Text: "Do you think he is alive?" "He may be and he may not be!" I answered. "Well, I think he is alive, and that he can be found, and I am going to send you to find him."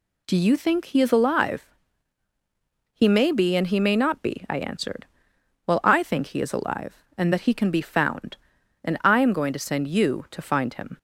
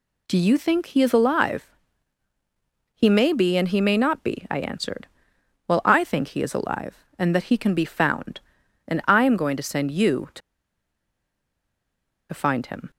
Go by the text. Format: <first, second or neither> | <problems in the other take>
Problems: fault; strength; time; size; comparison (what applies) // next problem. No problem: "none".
first | pauses between "to" and "find"; strong; at 10.4 s; 1.9 s long